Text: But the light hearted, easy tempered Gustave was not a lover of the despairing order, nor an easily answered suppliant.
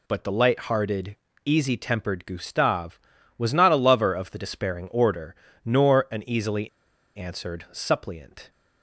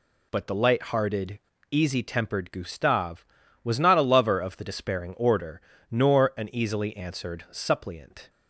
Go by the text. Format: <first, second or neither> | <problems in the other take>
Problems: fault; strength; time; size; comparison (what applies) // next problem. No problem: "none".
second | pauses between "easily" and "answered"; noticeable; at 6.6 s; 0.47 s long